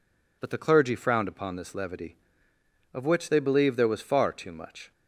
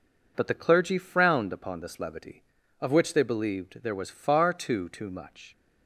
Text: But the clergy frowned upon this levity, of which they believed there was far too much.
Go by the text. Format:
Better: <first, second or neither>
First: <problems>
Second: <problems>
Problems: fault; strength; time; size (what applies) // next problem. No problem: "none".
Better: first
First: none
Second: says "too" twice; at 4.8 s